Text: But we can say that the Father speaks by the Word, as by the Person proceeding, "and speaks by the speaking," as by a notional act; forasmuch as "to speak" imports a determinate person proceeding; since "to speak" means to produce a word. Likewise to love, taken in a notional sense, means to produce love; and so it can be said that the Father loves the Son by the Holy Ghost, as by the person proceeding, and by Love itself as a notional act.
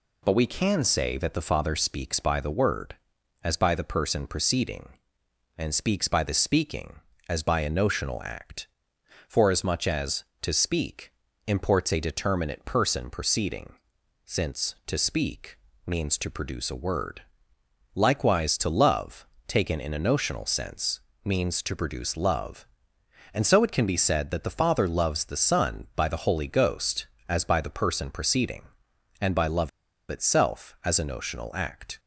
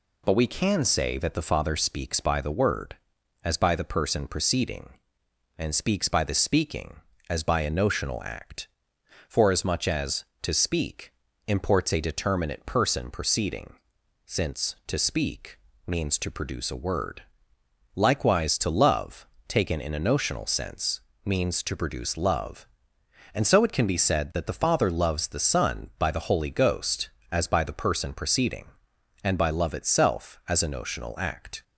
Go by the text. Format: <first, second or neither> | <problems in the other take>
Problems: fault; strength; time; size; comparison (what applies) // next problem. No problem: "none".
second | pauses between "speak" and "imports"; slight; at 11.1 s; 0.34 s long; slight in the second // pauses between "speak" and "means"; slight; at 15.5 s; 0.28 s long; slight in the second // pauses between "Love" and "itself"; at 29.6 s; 0.39 s long